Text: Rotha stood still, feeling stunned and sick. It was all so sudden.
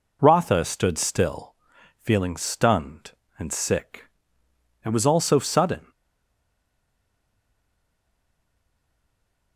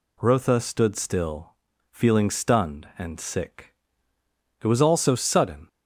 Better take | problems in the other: second | stays silent after the last word; strong; from 5.9 s on; 3.6 s long

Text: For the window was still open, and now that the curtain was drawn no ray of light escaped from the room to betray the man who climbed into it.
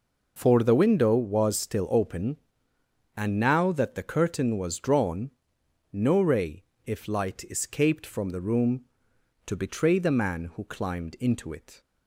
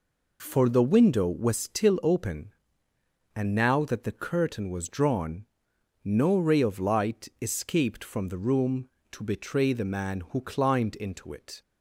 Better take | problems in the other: second | pauses between "drawn" and "no"; noticeable; at 5.3 s; 0.60 s long; noticeable in the second // says "if" for "of"; at 6.8 s

